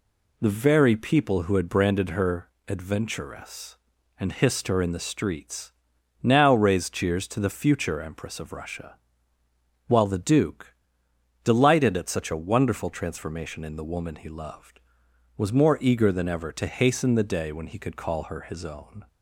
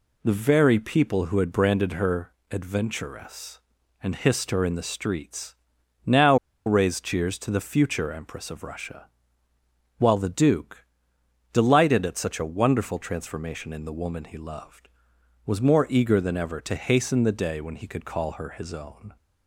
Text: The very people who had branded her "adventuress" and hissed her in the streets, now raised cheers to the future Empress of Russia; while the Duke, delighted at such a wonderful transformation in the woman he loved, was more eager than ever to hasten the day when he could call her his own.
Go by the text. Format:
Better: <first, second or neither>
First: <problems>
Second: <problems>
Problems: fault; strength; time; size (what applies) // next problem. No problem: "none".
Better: first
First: pauses between "her" and "adventuress"; slight; at 2.5 s; 0.18 s long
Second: pauses between "her" and "adventuress"; slight; at 2.3 s; 0.18 s long // pauses between "now" and "raised"; slight; at 6.3 s; 0.30 s long